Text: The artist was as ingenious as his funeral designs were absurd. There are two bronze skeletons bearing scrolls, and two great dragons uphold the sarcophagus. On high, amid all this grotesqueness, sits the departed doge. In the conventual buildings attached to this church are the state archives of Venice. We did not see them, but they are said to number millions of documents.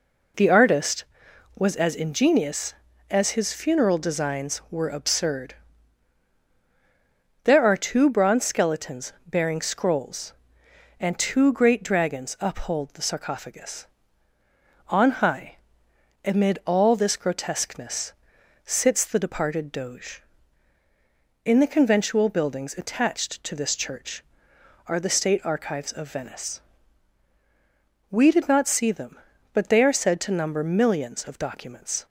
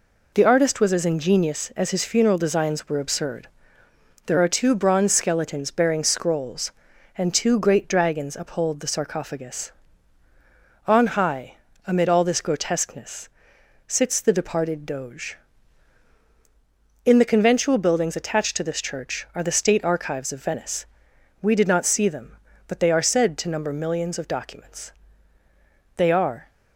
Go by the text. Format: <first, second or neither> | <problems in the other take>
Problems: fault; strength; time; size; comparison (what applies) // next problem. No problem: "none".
first | goes on to say "They are"; from 25.9 s on; 0.54 s long